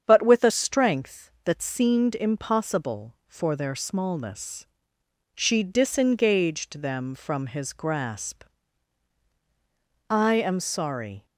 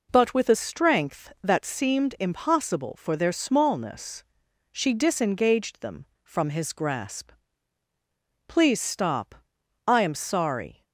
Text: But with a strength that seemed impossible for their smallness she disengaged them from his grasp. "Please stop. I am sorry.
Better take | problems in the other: second | starts louder than the rest; strong; until 1.0 s; 8 dB // pauses between "smallness" and "she"; noticeable; at 4.6 s; 0.70 s long; noticeable in the second // skips "Please stop"; at 9.2 s

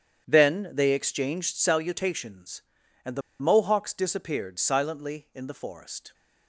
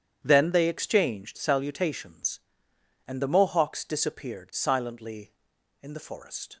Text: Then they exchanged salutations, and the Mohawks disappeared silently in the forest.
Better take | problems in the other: second | starts louder than the rest; strong; until 1.2 s; 8.5 dB; strong in the second // pauses between "the" and "Mohawks"; slight; at 3.2 s; 0.19 s long

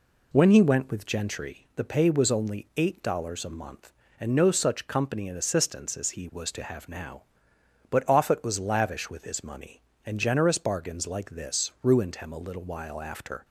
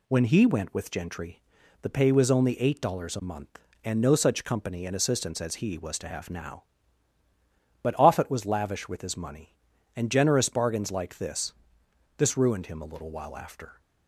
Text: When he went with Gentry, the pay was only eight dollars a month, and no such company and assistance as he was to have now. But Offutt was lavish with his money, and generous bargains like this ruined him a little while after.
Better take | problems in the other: first | says "this" twice; at 12.1 s

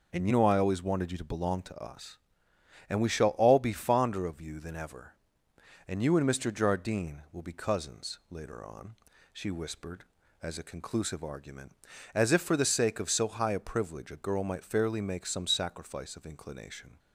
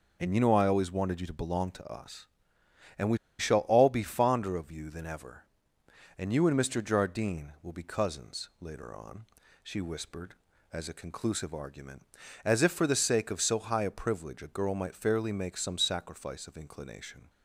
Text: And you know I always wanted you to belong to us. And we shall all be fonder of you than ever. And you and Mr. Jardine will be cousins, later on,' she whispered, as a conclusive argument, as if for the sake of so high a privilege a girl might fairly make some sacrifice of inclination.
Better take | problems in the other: first | pauses between "we" and "shall"; slight; at 3.1 s; 0.21 s long

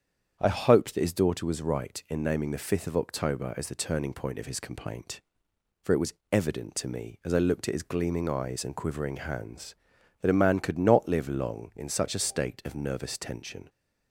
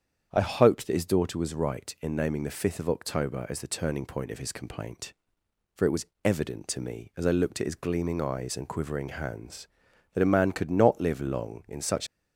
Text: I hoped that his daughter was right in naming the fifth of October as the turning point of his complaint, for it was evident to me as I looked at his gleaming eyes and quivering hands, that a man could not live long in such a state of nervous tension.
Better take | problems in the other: first | starts louder than the rest; strong; until 1.3 s; 8 dB; strong in the first // pauses between "was" and "evident"; slight; at 6.0 s; 0.16 s long; slight in the first // stops before "a state of nervous tension"; at 12.0 s

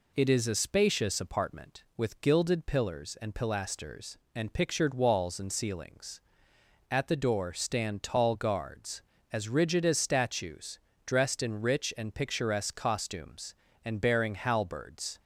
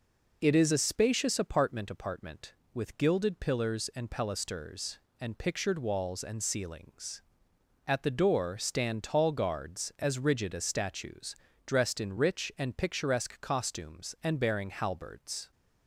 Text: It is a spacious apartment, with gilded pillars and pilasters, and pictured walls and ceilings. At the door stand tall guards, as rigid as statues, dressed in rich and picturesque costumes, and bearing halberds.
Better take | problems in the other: first | says "apartment" twice; at 1.9 s

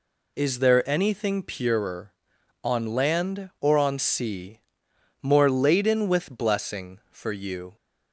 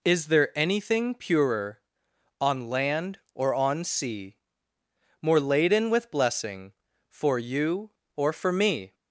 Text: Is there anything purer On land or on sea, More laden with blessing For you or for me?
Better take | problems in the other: second | stops before "or for me"; at 7.7 s

